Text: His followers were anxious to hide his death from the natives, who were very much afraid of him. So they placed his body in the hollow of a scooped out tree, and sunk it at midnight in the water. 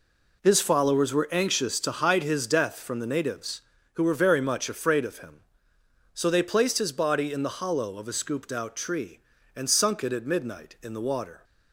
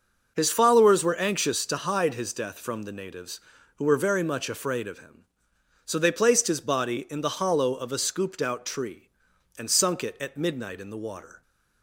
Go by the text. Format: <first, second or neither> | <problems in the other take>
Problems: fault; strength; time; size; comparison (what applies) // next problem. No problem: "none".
neither | none